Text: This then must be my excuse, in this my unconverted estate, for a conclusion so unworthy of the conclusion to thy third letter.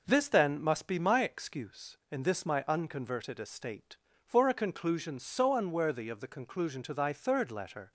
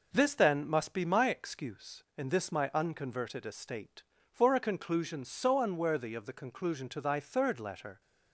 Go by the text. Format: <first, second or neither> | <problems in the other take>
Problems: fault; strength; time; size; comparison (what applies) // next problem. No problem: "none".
neither | none